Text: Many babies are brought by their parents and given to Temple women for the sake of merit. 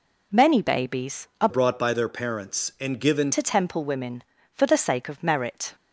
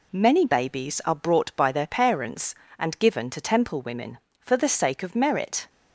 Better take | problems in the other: second | changes voice from "brought" to "given"; from 1.4 to 3.3 s; 1.9 s long

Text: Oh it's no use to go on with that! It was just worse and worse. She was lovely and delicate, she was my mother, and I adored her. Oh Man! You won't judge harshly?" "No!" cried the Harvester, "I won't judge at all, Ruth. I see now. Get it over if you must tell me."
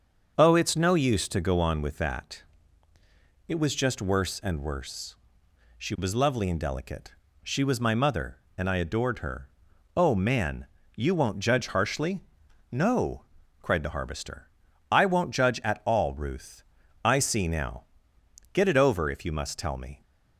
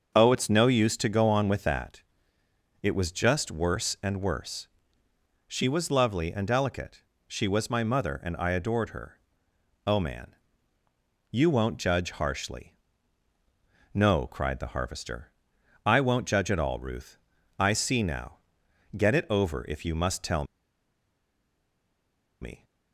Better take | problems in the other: first | starts louder than the rest; until 1.1 s; 6.5 dB; also in the first // pauses between "tell" and "me"; strong; at 20.4 s; 1.9 s long

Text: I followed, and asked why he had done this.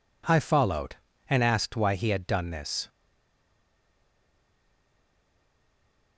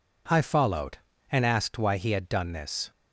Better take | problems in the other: second | stays silent after the last word; strong; from 2.8 s on; 3.3 s long

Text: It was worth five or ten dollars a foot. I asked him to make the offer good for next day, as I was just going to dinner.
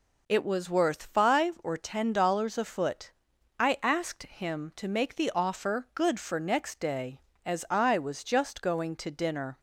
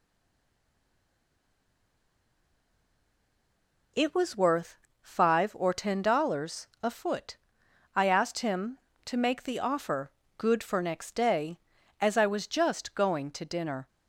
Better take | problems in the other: first | stays silent before the first word; strong; until 3.9 s; 3.9 s long // pauses between "worth" and "five"; slight; at 4.7 s; 0.26 s long // pauses between "dollars" and "a"; slight; at 6.6 s; 0.16 s long // pauses between "offer" and "good"; slight; at 10.0 s; 0.26 s long

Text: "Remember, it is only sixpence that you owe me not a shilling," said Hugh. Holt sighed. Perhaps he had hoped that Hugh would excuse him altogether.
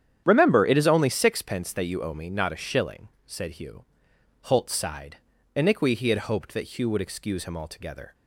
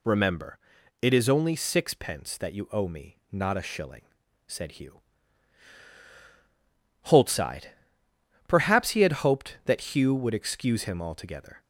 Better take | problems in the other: second | starts louder than the rest; strong; until 1.2 s; 9.5 dB // says "Iniqui" for "Perhaps"; at 5.5 s

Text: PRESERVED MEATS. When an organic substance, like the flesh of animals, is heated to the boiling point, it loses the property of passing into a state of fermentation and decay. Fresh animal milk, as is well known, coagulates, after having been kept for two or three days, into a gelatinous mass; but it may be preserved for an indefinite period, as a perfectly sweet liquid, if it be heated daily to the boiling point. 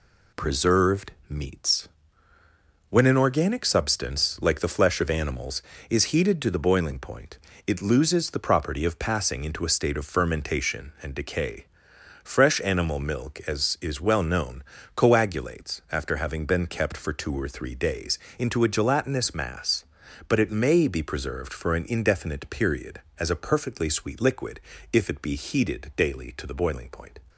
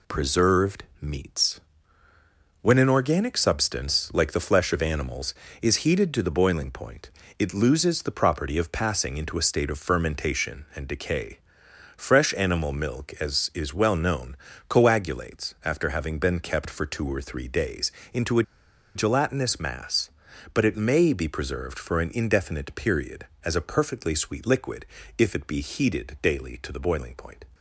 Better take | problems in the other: first | pauses between "PRESERVED" and "MEATS"; slight; at 0.8 s; 0.16 s long; slight in the first // pauses between "a" and "gelatinous"; noticeable; at 18.4 s; 0.52 s long

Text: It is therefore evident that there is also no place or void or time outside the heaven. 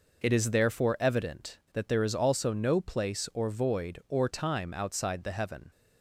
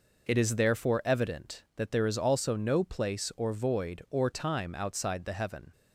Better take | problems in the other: neither | none

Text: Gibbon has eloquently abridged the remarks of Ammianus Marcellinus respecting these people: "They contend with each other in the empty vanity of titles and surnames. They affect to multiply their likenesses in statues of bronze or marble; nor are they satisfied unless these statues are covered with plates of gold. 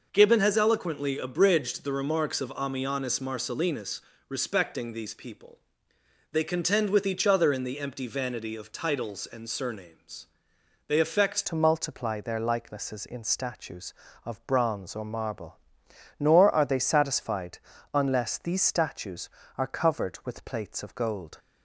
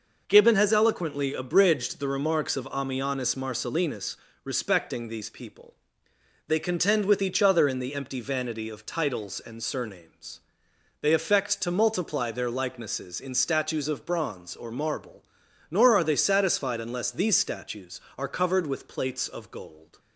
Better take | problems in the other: second | pauses between "Marcellinus" and "respecting"; slight; at 3.9 s; 0.28 s long; slight in the second // changes voice at "to"; from 11.4 s on; 9.9 s long // pauses between "satisfied" and "unless"; slight; at 17.5 s; 0.36 s long

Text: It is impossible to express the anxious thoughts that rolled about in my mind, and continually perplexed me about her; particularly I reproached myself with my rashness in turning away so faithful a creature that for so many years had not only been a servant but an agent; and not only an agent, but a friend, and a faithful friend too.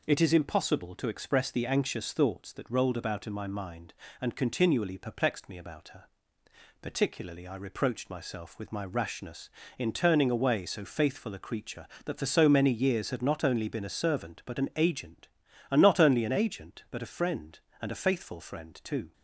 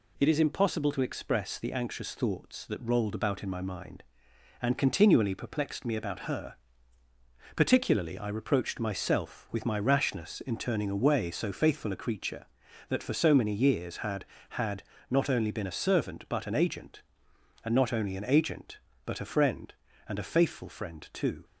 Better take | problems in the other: first | says "had" twice; at 14.4 s

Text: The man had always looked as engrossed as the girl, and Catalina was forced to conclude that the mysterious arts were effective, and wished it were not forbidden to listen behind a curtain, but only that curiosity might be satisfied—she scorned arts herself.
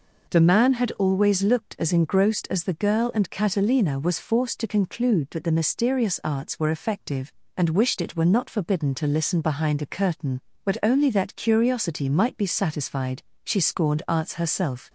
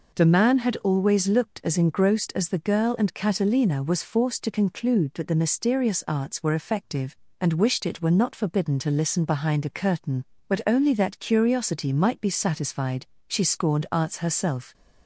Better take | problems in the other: neither | none

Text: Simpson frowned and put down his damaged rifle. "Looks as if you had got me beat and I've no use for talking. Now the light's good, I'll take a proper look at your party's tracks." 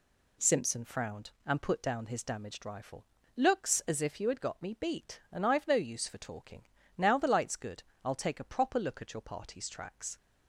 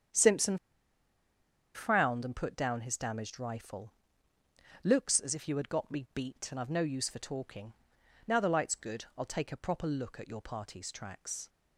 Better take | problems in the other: first | starts louder than the rest; strong; until 2.3 s; 8.5 dB // pauses between "Simpson" and "frowned"; at 0.5 s; 1.1 s long

